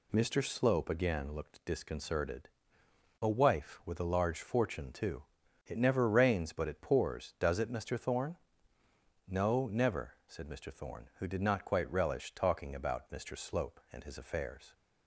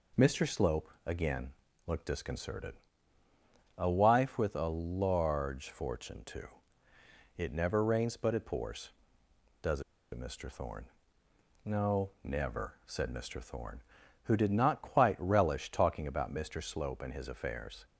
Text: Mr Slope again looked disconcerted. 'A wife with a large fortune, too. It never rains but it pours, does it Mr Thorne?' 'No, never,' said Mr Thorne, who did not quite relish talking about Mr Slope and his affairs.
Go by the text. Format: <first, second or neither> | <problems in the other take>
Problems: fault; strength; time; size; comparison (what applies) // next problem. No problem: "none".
first | pauses between "Slope" and "again"; slight; at 0.8 s; 0.16 s long // pauses between "again" and "looked"; at 1.5 s; 0.38 s long // pauses between "does" and "it"; slight; at 9.8 s; 0.31 s long